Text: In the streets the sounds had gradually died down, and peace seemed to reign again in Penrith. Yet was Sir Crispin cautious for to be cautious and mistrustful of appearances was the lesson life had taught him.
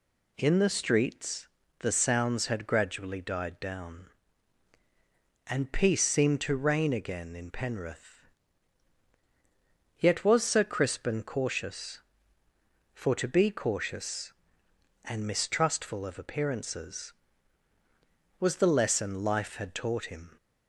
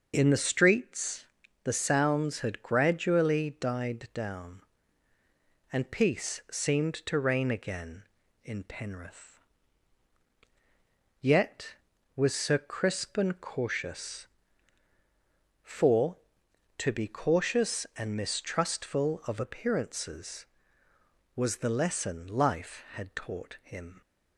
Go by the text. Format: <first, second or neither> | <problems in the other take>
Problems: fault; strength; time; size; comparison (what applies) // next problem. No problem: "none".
neither | pauses between "streets" and "the"; the same in both